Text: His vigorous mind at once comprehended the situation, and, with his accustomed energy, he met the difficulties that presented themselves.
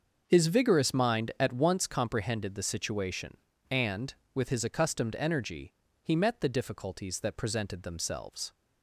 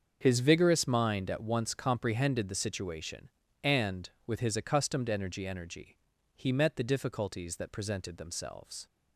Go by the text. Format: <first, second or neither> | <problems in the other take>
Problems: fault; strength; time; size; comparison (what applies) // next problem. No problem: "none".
first | starts louder than the rest; until 1.2 s; 6.5 dB; also in the first // says "energy" twice; at 5.4 s